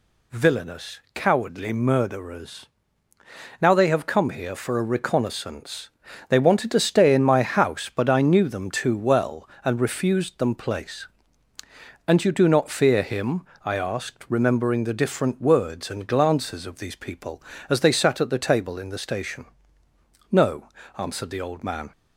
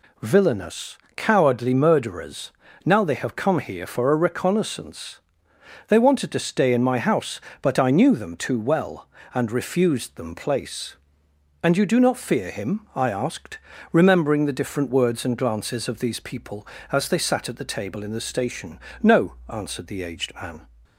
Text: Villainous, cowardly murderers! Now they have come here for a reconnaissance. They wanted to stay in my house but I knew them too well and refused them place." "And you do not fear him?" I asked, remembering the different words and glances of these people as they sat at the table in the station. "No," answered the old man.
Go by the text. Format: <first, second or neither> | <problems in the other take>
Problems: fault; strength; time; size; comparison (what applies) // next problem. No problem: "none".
first | says "aged" for "old"; at 20.0 s